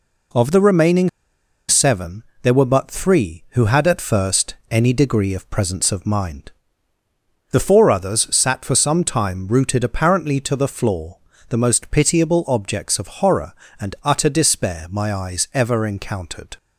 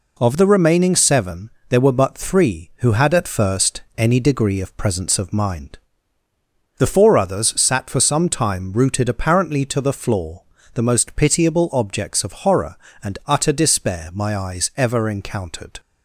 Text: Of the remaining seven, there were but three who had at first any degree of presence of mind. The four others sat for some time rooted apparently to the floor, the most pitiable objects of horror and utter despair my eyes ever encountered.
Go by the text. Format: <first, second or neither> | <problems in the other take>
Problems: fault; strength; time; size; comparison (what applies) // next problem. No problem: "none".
second | pauses between "remaining" and "seven"; noticeable; at 1.0 s; 0.59 s long